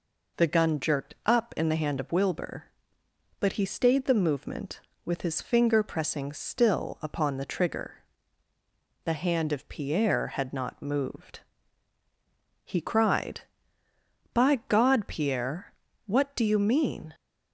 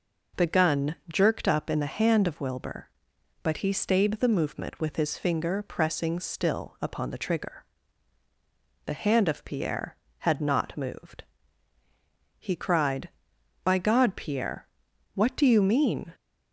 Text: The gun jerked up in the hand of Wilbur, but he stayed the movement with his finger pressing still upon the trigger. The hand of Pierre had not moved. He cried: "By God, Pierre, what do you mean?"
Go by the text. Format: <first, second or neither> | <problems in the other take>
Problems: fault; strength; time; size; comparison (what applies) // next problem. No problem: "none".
neither | none